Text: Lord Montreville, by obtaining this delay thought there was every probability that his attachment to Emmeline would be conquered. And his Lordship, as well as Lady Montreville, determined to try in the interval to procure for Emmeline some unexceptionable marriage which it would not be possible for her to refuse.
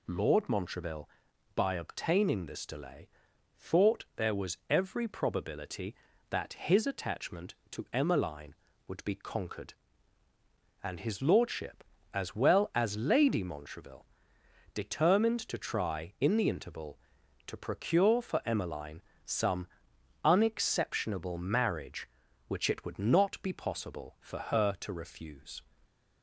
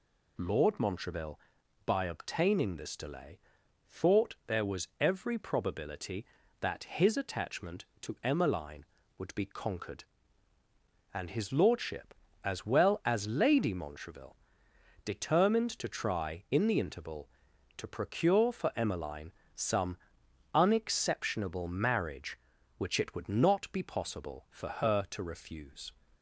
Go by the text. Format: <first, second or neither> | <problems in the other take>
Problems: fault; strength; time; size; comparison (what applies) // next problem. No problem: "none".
neither | pauses between "delay" and "thought"; noticeable; the same in both // pauses between "Emmeline" and "some"; slight; the same in both // pauses between "some" and "unexceptionable"; noticeable; the same in both